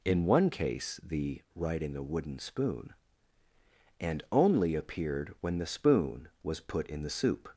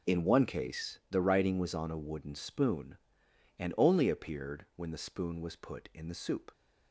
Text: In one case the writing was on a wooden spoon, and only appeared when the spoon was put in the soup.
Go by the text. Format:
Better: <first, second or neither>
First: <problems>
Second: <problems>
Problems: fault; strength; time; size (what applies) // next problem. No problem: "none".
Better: second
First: skips "was on"; at 1.9 s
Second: none